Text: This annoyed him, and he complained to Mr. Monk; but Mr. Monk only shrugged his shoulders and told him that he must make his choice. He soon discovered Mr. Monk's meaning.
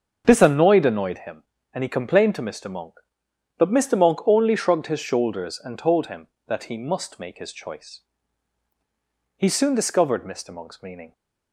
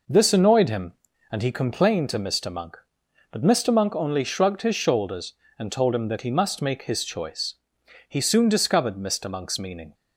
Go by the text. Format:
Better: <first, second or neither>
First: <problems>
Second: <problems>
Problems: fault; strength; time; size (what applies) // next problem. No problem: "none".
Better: second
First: starts louder than the rest; until 1.2 s; 7 dB // says "annoyed" twice; at 0.8 s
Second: none